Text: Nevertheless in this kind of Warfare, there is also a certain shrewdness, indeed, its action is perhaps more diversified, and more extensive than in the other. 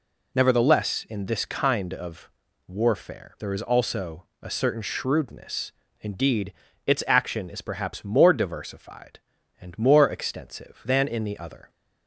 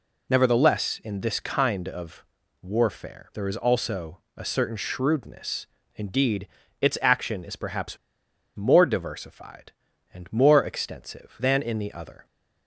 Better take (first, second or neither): first